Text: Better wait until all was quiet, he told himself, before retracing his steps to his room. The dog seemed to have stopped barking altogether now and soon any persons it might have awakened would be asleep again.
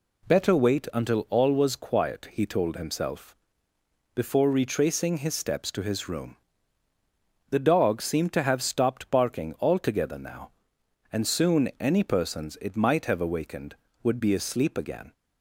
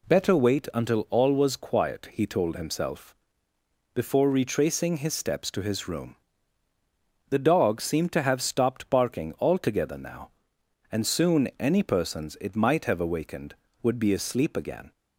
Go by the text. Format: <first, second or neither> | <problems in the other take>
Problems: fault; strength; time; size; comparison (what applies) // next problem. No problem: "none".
neither | none